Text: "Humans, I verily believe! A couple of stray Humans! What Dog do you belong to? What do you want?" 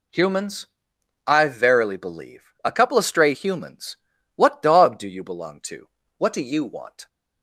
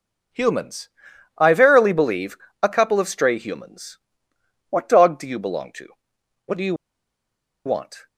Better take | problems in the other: first | pauses between "you" and "want"; noticeable; at 6.7 s; 0.92 s long

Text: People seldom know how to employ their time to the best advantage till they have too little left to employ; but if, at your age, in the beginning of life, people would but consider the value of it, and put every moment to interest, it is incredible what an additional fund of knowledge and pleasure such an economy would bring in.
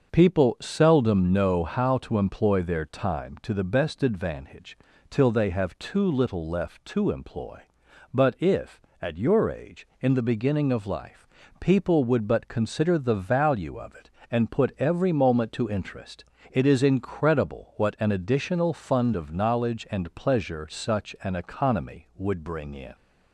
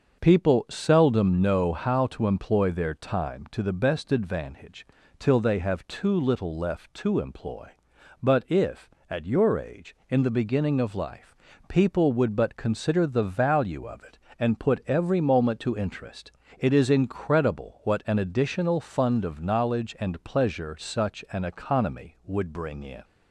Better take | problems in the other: neither | starts louder than the rest; the same in both // pauses between "advantage" and "till"; slight; the same in both

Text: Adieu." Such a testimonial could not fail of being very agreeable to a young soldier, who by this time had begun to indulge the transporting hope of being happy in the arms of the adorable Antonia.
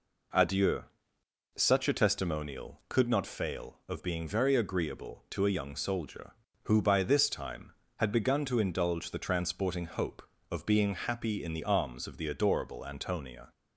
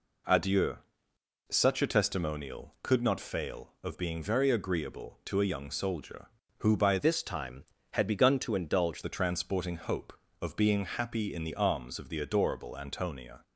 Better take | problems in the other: first | changes voice from "this" to "indulge"; from 6.9 to 9.0 s; 2.1 s long

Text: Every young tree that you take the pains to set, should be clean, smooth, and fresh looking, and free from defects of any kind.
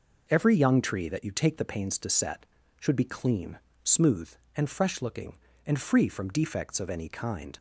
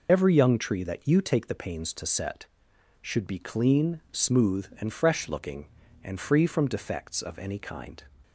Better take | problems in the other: first | loses the start of "Every"; at 0.0 s; 30 ms

